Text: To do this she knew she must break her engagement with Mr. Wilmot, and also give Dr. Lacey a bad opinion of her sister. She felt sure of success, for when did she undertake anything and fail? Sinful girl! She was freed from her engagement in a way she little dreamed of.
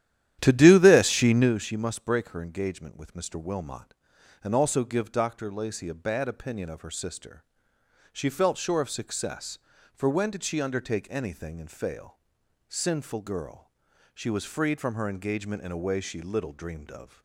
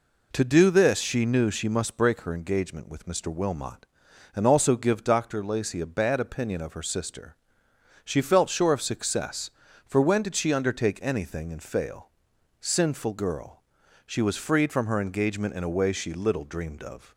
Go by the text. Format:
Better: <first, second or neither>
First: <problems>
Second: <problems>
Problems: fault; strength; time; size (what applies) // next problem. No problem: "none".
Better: second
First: starts louder than the rest; strong; until 1.5 s; 11.5 dB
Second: none